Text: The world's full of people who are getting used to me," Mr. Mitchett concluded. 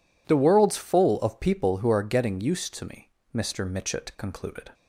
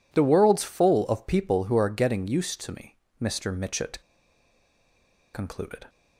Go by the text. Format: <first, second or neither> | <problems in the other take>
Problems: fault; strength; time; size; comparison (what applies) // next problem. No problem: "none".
first | pauses between "Mitchett" and "concluded"; strong; at 3.9 s; 1.3 s long